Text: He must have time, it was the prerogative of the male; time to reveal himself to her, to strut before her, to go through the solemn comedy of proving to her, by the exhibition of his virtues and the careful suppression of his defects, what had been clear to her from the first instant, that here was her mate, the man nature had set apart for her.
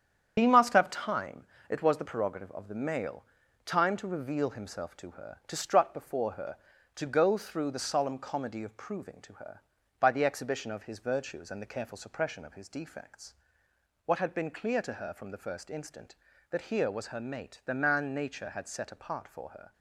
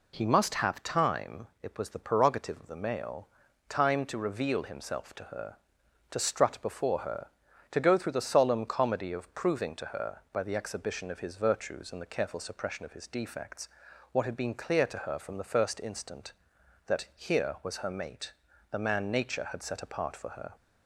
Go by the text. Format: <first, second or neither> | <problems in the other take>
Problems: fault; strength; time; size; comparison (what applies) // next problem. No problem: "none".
second | loses the start of "He"; at 0.3 s; 60 ms // starts louder than the rest; strong; until 1.3 s; 8.5 dB